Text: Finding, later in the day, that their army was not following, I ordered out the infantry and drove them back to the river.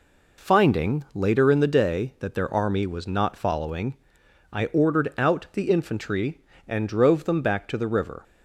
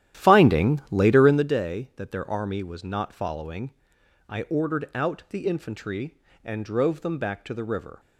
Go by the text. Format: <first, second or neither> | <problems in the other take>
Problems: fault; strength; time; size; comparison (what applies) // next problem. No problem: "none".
first | starts louder than the rest; strong; until 1.5 s; 12 dB